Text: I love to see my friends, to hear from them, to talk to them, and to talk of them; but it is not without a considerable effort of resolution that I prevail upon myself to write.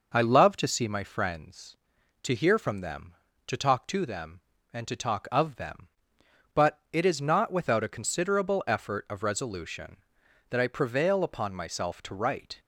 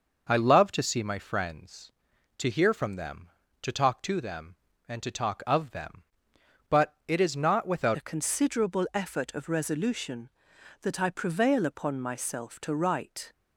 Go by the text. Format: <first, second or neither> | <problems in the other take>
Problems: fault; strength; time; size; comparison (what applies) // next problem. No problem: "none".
first | changes voice at "a"; from 7.9 s on; 5.4 s long